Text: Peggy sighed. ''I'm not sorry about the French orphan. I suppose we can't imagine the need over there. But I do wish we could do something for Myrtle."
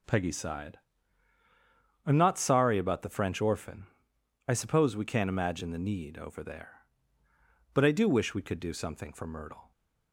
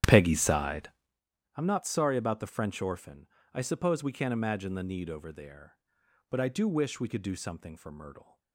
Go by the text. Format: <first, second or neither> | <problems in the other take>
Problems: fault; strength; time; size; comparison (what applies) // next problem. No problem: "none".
first | starts louder than the rest; strong; until 1.2 s; 11 dB